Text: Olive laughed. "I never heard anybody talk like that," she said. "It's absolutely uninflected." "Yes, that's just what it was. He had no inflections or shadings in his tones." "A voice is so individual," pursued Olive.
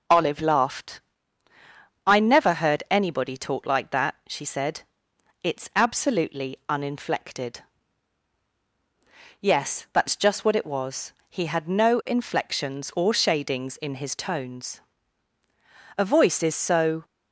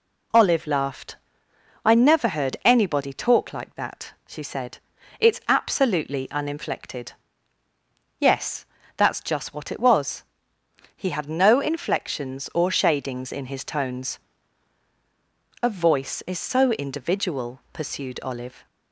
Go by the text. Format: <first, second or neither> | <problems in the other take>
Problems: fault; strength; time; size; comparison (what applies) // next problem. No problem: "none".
second | stops before "individual pursued Olive"; at 17.0 s